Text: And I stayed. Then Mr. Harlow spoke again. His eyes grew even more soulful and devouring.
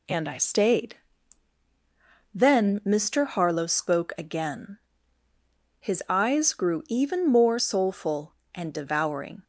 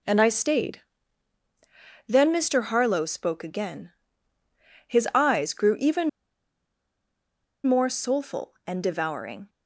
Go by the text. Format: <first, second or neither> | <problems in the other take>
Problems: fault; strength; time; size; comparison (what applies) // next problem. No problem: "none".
first | pauses between "even" and "more"; strong; at 6.0 s; 1.5 s long